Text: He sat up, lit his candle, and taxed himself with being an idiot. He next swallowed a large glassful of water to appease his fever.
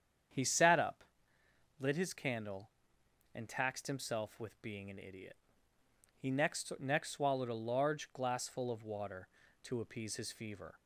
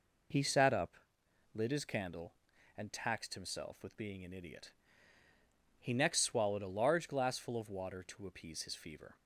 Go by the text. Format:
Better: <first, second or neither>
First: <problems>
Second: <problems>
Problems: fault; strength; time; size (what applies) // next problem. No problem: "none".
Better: second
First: starts louder than the rest; strong; until 2.0 s; 8 dB // says "next" twice; at 6.7 s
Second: none